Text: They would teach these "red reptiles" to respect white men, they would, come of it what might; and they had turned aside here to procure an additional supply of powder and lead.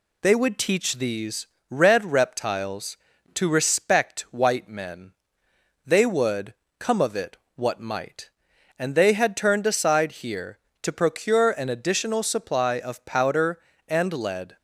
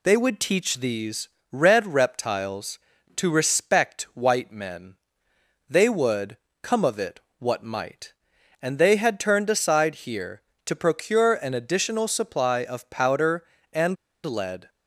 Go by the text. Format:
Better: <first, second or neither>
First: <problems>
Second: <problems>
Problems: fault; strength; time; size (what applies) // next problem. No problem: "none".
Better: first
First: pauses between "these" and "red"; slight; at 1.4 s; 0.22 s long // pauses between "it" and "what"; slight; at 7.3 s; 0.20 s long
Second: pauses between "these" and "red"; slight; at 1.2 s; 0.22 s long // pauses between "it" and "what"; slight; at 7.1 s; 0.20 s long // pauses between "and" and "lead"; slight; at 13.9 s; 0.28 s long